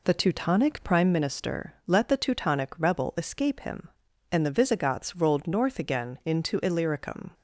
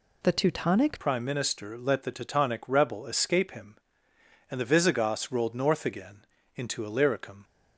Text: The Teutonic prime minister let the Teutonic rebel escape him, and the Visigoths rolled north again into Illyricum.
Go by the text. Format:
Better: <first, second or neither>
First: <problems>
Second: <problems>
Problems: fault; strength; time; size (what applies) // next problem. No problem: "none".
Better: first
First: none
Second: changes voice at "prime"; from 1.0 s on; 6.4 s long // pauses between "again" and "into"; slight; at 6.2 s; 0.32 s long